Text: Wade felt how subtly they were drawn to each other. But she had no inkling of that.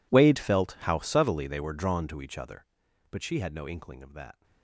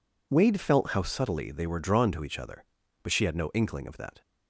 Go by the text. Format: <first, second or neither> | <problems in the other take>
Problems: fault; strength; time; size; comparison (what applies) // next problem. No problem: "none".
second | gets quieter; strong; throughout; 21 dB